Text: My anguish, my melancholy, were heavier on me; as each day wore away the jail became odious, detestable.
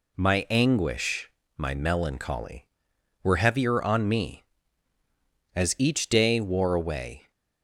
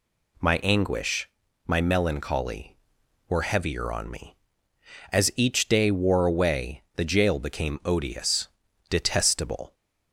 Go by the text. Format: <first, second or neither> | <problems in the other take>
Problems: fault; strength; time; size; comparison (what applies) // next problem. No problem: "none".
second | stops before "the jail became odious detestable"; at 7.3 s